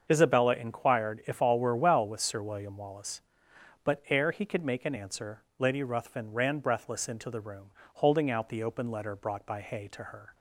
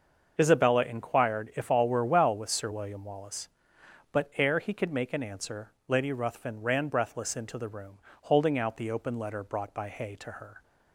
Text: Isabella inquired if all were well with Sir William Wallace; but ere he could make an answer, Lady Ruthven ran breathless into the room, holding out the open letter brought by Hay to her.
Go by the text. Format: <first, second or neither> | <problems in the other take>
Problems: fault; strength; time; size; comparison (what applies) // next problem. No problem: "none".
neither | starts louder than the rest; the same in both